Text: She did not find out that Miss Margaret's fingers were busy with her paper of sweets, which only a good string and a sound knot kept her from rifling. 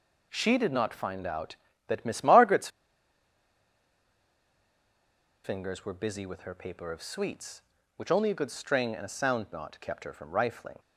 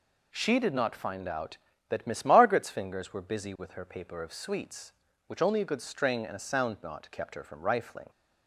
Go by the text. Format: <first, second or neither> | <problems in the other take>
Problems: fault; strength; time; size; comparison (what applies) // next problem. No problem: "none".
second | pauses between "Margaret's" and "fingers"; strong; at 2.6 s; 2.7 s long